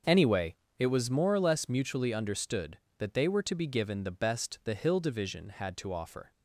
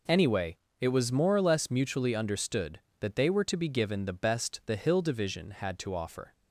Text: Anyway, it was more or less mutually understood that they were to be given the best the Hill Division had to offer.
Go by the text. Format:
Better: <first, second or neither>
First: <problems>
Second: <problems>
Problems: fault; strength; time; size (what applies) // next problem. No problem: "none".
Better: second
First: starts louder than the rest; until 0.9 s; 6.5 dB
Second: none